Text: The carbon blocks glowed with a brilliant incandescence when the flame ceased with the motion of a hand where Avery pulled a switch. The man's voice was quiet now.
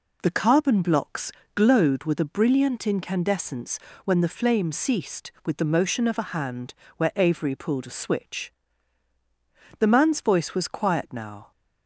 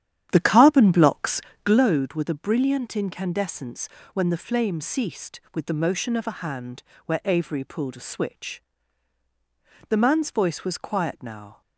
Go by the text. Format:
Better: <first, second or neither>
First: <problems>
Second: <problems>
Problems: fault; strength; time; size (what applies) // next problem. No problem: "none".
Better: first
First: pauses between "blocks" and "glowed"; slight; at 1.2 s; 0.24 s long // pauses between "incandescence" and "when"; slight; at 3.7 s; 0.28 s long // pauses between "hand" and "where"; slight; at 6.7 s; 0.22 s long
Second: starts louder than the rest; strong; until 1.9 s; 10 dB // pauses between "blocks" and "glowed"; slight; at 1.3 s; 0.24 s long // pauses between "incandescence" and "when"; slight; at 3.8 s; 0.27 s long // pauses between "hand" and "where"; slight; at 6.8 s; 0.22 s long